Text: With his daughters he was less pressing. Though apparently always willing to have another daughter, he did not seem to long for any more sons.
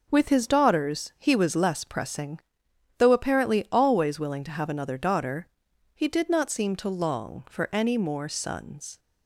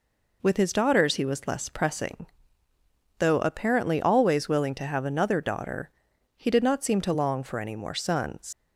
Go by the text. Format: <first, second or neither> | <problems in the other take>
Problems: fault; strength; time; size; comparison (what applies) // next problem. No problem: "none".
first | leaves "sons" unfinished; at 8.5 s; 120 ms